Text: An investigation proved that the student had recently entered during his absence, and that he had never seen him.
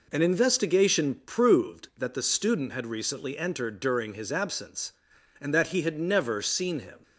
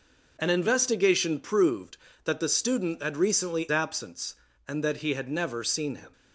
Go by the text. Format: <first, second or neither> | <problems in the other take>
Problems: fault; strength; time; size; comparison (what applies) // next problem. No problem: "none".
first | skips "entered during his"; at 3.6 s